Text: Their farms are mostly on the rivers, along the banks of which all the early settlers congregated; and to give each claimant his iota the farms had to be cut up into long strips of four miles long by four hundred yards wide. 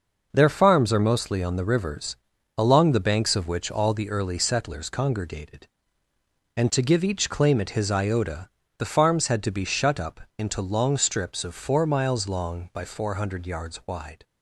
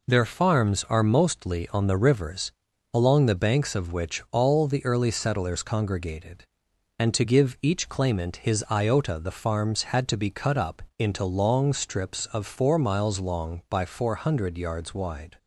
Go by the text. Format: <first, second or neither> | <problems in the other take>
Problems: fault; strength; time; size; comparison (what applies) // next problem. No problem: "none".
second | pauses between "iota" and "the"; slight; at 8.4 s; 0.30 s long // says "shut" for "cut"; at 9.6 s // pauses between "up" and "into"; slight; at 10.2 s; 0.16 s long; slight in the second